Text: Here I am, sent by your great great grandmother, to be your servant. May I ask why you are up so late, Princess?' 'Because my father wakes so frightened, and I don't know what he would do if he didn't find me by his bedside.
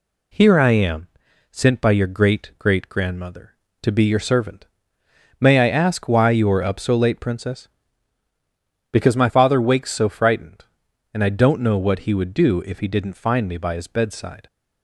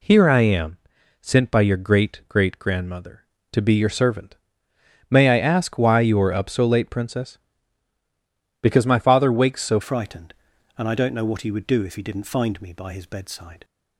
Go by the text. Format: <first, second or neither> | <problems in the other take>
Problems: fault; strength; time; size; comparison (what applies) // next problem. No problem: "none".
first | changes voice at "frightened"; from 9.8 s on; 3.8 s long